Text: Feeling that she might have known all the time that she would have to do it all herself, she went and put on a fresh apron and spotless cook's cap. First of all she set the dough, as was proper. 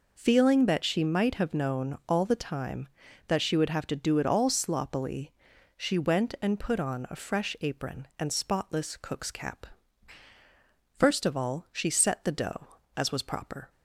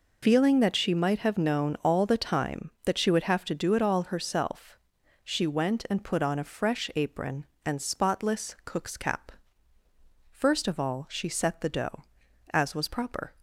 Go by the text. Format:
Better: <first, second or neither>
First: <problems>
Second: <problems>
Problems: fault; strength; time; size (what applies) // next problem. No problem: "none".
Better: second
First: says "sloppily" for "herself"; at 4.4 s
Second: none